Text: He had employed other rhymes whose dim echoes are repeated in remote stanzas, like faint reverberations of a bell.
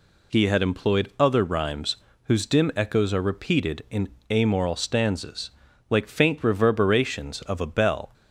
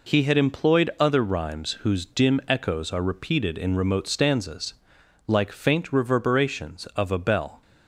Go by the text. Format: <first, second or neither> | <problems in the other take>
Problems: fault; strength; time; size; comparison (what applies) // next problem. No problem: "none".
second | pauses between "rhymes" and "whose"; slight; at 1.9 s; 0.26 s long // says "amoral" for "remote"; at 4.3 s